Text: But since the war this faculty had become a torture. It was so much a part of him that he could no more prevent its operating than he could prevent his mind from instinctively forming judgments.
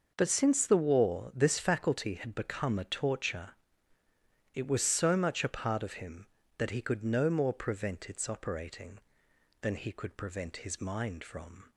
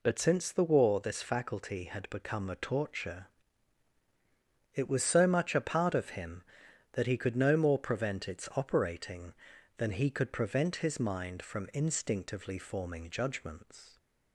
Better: second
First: stops before "instinctively forming judgments"; at 11.7 s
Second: none

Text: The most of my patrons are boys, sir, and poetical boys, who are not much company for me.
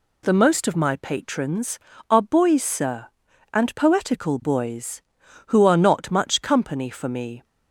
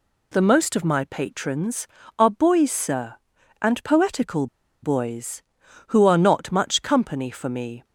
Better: first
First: none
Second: pauses between "poetical" and "boys"; slight; at 4.4 s; 0.36 s long

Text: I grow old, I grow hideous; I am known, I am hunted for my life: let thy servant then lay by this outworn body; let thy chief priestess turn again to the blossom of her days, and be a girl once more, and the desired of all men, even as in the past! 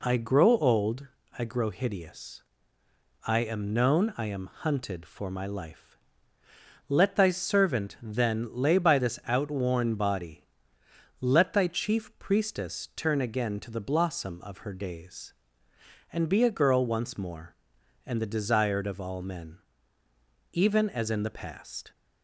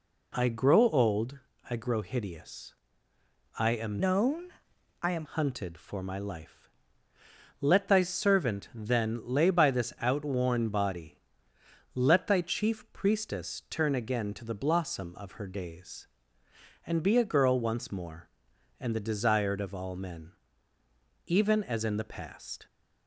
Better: first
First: none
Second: changes voice from "known" to "am"; from 3.9 to 5.2 s; 1.3 s long

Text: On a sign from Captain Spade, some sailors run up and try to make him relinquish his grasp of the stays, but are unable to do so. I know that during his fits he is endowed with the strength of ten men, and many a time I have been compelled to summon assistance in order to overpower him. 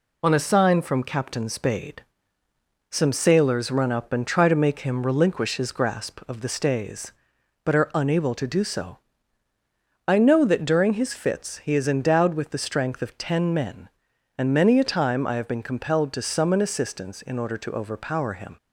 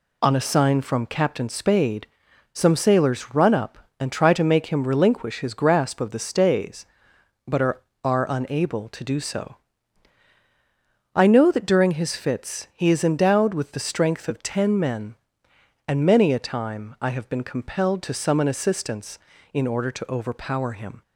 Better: first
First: none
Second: says "are" twice; at 8.0 s

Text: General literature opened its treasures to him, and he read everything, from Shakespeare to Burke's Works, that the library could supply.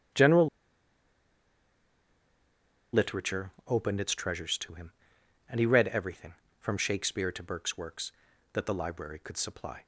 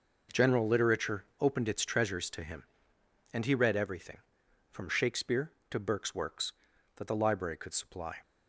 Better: second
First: starts louder than the rest; strong; until 3.7 s; 9 dB // pauses between "General" and "literature"; strong; at 0.4 s; 2.4 s long // pauses between "literature" and "opened"; slight; at 3.5 s; 0.16 s long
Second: pauses between "literature" and "opened"; slight; at 1.2 s; 0.15 s long

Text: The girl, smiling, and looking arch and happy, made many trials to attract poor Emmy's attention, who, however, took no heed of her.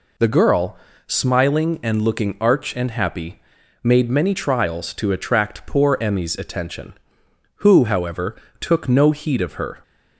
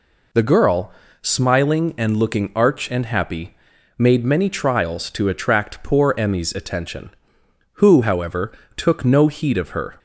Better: neither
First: none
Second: none

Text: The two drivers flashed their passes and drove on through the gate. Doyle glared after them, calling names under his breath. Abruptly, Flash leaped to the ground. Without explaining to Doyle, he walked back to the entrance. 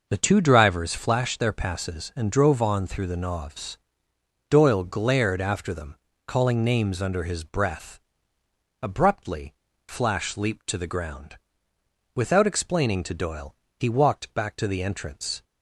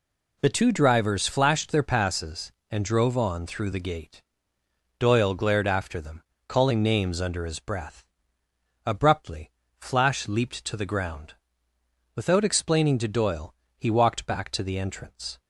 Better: second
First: says "novs" for "gate"; at 3.1 s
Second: none

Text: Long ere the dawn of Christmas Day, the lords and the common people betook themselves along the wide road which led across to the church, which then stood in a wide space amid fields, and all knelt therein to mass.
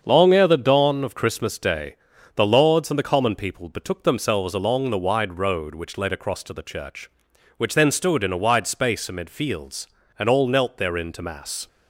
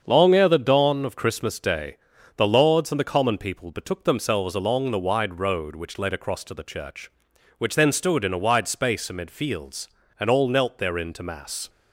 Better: neither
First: starts louder than the rest; until 1.0 s; 7 dB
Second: starts louder than the rest; until 1.0 s; 7 dB

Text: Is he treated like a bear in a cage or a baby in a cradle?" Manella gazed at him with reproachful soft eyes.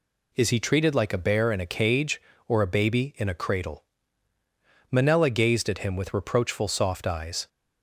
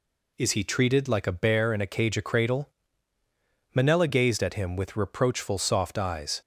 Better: first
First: none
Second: skips "or a baby in"; at 2.1 s

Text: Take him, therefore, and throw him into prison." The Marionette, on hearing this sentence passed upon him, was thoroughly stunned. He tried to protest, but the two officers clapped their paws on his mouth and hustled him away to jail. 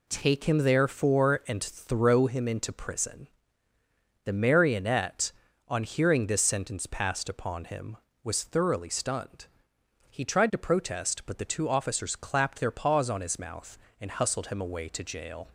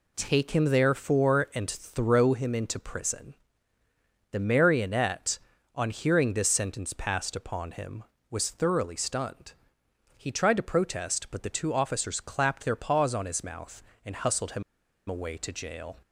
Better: first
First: none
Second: pauses between "him" and "away"; noticeable; at 14.6 s; 0.46 s long

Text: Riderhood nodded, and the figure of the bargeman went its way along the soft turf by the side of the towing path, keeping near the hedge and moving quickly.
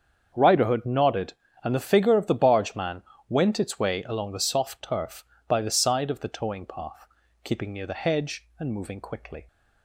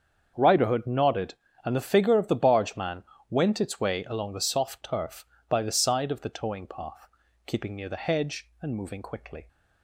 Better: neither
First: starts louder than the rest; strong; until 1.3 s; 7.5 dB // pauses between "bargeman" and "went"; slight; at 3.0 s; 0.26 s long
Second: starts louder than the rest; strong; until 1.3 s; 7.5 dB // pauses between "bargeman" and "went"; slight; at 3.0 s; 0.26 s long

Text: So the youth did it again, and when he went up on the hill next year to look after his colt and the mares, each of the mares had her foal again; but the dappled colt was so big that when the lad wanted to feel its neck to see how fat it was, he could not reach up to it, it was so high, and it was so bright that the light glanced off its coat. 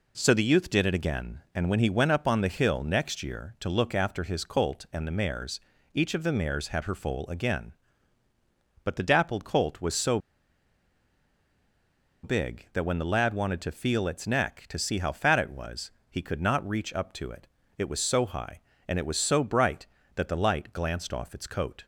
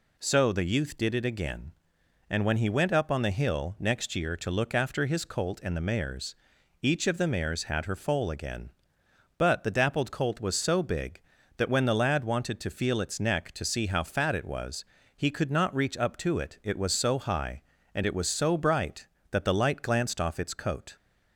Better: second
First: pauses between "so" and "big"; strong; at 10.1 s; 2.0 s long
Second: none

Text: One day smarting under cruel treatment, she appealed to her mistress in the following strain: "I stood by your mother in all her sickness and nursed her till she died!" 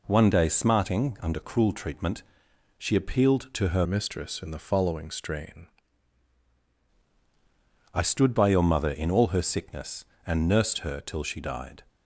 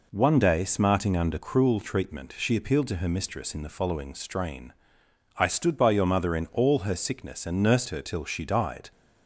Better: second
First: changes voice from "mistress" to "strain"; from 3.8 to 5.6 s; 1.8 s long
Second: none

